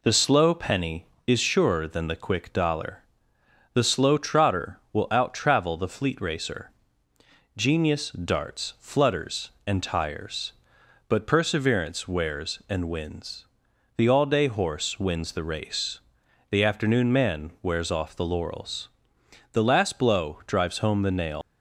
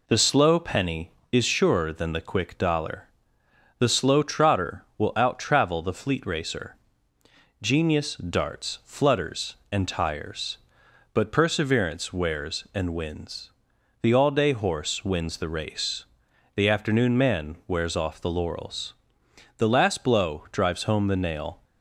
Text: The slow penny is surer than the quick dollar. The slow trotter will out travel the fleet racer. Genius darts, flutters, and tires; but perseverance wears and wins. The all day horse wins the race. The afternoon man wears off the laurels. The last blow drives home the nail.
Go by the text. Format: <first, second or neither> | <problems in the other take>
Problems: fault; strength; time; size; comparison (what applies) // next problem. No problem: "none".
second | leaves "nail" unfinished; at 21.4 s; 175 ms